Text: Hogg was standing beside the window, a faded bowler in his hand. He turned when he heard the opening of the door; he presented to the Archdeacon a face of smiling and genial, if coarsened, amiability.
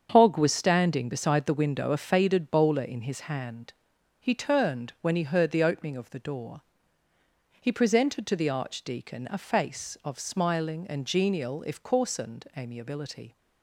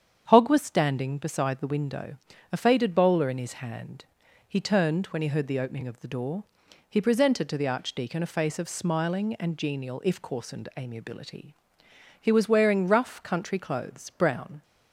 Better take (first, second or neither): first